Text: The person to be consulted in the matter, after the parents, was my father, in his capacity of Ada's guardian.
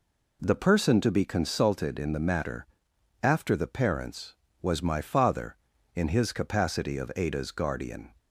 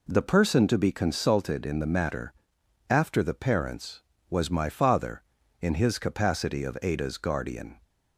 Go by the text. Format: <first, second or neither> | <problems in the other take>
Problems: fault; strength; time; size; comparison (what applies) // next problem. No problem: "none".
neither | none